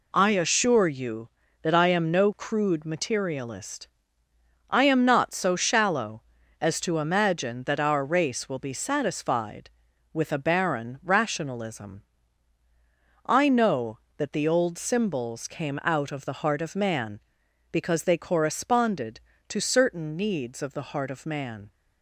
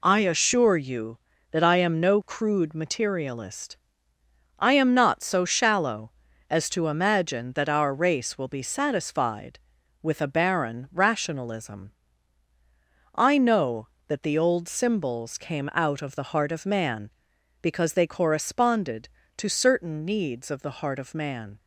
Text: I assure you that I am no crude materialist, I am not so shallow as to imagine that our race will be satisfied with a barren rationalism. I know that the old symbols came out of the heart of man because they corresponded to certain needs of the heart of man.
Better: neither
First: none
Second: none

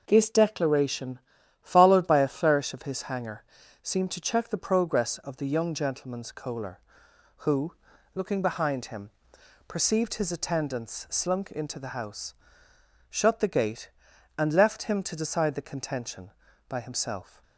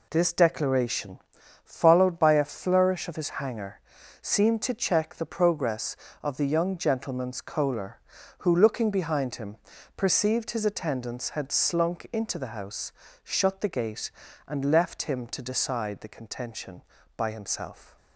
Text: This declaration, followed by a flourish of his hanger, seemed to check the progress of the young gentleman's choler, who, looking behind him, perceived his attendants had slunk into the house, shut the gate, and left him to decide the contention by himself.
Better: second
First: skips "had"; at 11.0 s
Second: none

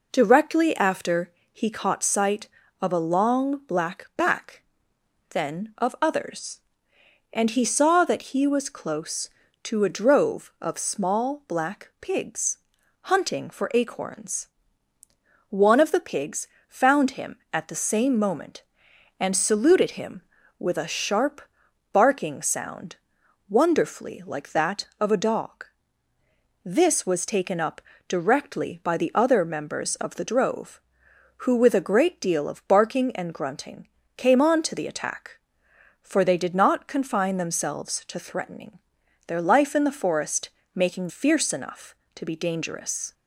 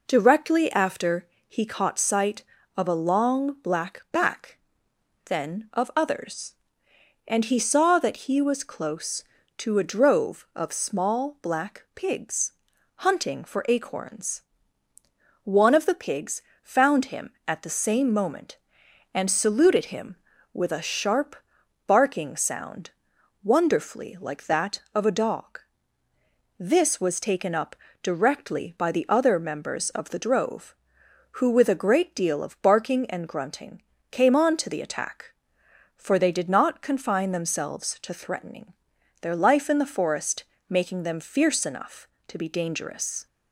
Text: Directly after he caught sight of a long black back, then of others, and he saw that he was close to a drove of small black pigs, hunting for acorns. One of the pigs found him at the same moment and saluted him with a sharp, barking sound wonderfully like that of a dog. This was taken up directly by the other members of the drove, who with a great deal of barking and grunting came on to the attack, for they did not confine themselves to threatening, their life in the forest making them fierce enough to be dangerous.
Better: second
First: pauses between "after" and "he"; slight; at 1.2 s; 0.22 s long // pauses between "pigs" and "found"; slight; at 16.4 s; 0.20 s long // pauses between "sound" and "wonderfully"; noticeable; at 22.9 s; 0.52 s long // pauses between "up" and "directly"; slight; at 27.8 s; 0.26 s long // pauses between "grunting" and "came"; slight; at 33.8 s; 0.28 s long // pauses between "forest" and "making"; slight; at 40.4 s; 0.26 s long // skips "them"; at 41.0 s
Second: pauses between "after" and "he"; slight; at 1.2 s; 0.22 s long // pauses between "pigs" and "found"; slight; at 16.4 s; 0.20 s long // pauses between "sound" and "wonderfully"; noticeable; at 22.9 s; 0.52 s long // pauses between "up" and "directly"; slight; at 27.7 s; 0.26 s long // pauses between "grunting" and "came"; slight; at 33.8 s; 0.28 s long // pauses between "forest" and "making"; slight; at 40.4 s; 0.26 s long

